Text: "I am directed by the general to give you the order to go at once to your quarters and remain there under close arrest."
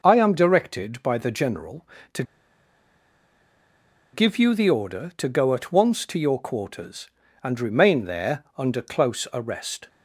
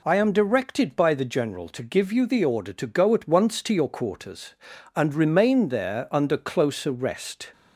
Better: second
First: pauses between "to" and "give"; strong; at 2.2 s; 1.9 s long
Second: none

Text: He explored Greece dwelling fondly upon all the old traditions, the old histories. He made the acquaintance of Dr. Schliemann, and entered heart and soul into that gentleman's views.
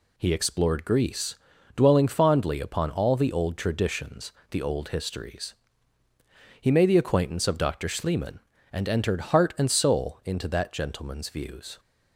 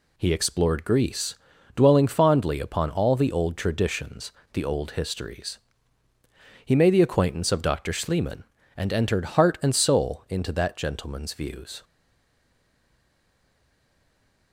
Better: first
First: pauses between "Greece" and "dwelling"; at 1.3 s; 0.40 s long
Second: pauses between "Greece" and "dwelling"; at 1.3 s; 0.40 s long // stays silent after the last word; strong; from 11.8 s on; 2.7 s long

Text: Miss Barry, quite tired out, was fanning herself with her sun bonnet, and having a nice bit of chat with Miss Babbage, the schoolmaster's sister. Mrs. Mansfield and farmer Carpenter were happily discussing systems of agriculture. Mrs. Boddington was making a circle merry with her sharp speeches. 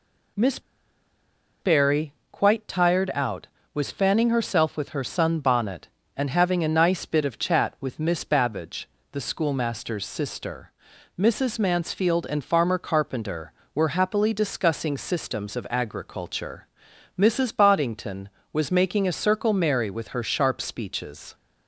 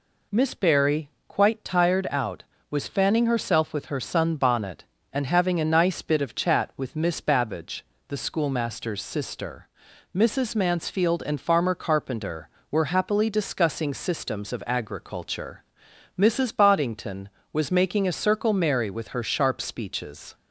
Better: second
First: pauses between "Miss" and "Barry"; at 0.5 s; 1.0 s long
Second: none

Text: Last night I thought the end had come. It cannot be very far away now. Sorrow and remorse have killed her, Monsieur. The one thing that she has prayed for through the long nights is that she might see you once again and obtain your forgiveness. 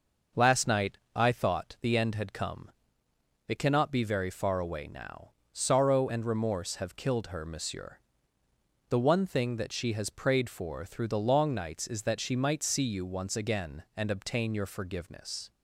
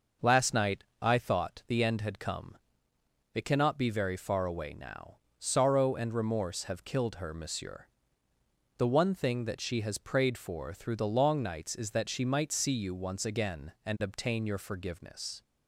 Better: neither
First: pauses between "night" and "I"; slight; at 0.9 s; 0.18 s long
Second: pauses between "night" and "I"; slight; at 0.8 s; 0.18 s long

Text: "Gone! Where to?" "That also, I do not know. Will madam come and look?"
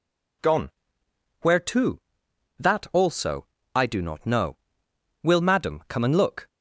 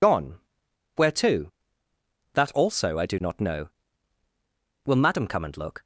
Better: first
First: none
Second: loses the start of "Gone"; at 0.0 s; 55 ms

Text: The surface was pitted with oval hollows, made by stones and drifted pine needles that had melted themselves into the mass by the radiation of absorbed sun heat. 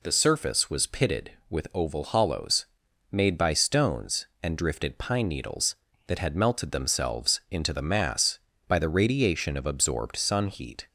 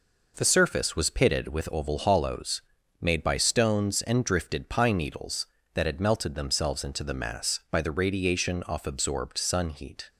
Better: first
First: none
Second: says "off" for "of"; at 8.6 s

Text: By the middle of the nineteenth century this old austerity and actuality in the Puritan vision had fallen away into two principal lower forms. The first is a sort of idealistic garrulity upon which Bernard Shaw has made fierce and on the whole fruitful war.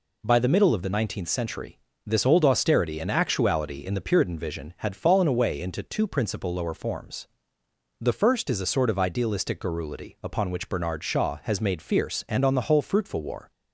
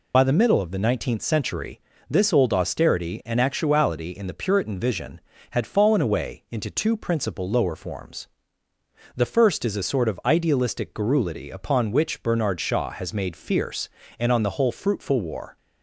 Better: first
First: pauses between "century" and "this"; slight; at 1.7 s; 0.26 s long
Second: loses the start of "By"; at 0.1 s; 35 ms // pauses between "century" and "this"; slight; at 1.7 s; 0.30 s long

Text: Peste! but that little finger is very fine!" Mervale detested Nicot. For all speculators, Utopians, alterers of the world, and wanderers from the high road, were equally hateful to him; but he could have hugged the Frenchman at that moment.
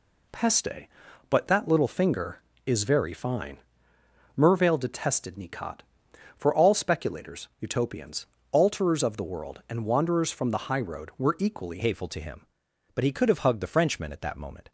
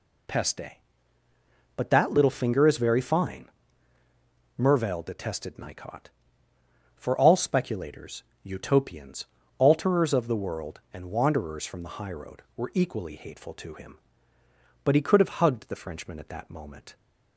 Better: second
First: changes voice at "hateful"; from 11.8 s on; 2.9 s long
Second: none

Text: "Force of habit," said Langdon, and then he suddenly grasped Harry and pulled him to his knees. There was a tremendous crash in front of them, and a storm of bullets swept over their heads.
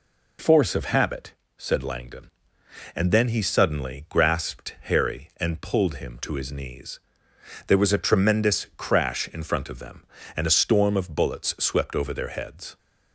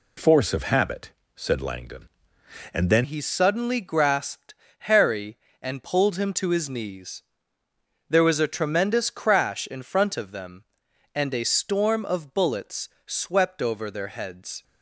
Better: first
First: none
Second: changes voice at "he"; from 3.0 s on; 11.6 s long // pauses between "grasped" and "Harry"; slight; at 4.5 s; 0.24 s long // pauses between "bullets" and "swept"; slight; at 12.8 s; 0.18 s long

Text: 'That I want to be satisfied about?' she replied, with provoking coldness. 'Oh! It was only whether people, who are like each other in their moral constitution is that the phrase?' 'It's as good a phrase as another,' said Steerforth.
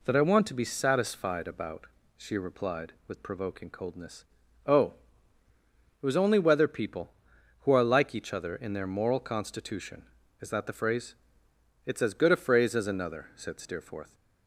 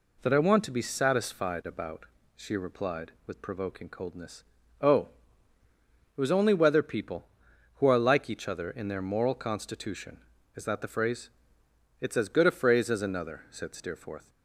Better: neither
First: none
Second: none

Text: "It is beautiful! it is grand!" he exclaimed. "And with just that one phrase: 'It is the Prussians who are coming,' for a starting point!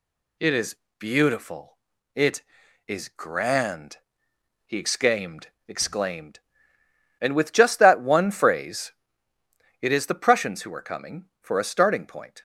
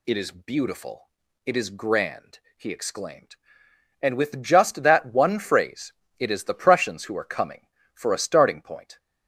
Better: second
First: pauses between "is" and "beautiful"; slight; at 0.7 s; 0.22 s long // says "exclaimed" twice; at 5.6 s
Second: none

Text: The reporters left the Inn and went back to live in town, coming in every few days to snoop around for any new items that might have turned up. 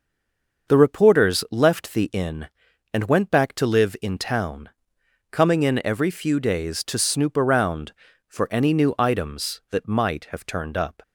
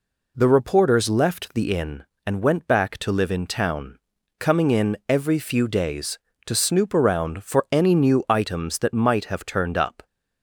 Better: second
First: stays silent before the first word; slight; until 0.6 s; 0.6 s long // starts louder than the rest; until 1.7 s; 6 dB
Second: none

